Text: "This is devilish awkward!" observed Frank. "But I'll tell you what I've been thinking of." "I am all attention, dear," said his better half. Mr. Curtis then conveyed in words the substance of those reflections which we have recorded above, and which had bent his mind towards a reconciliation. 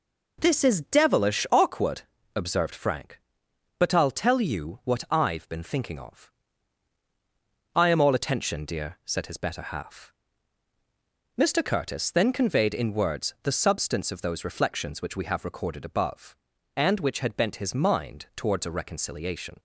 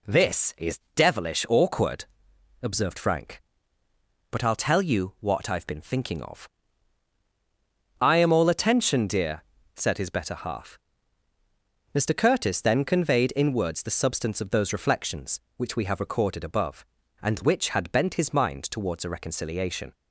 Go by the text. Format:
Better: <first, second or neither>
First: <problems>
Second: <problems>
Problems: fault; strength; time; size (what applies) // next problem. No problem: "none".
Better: neither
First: none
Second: none